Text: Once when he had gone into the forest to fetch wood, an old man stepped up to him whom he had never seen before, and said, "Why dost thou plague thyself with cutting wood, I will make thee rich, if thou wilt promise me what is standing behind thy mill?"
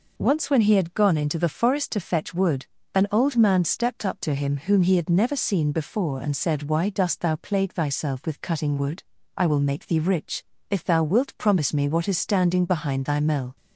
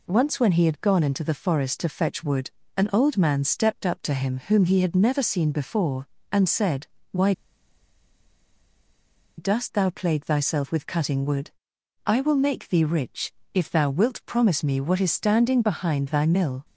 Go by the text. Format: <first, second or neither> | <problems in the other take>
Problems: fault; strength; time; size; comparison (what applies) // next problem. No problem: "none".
first | pauses between "Why" and "dost"; strong; at 7.3 s; 2.0 s long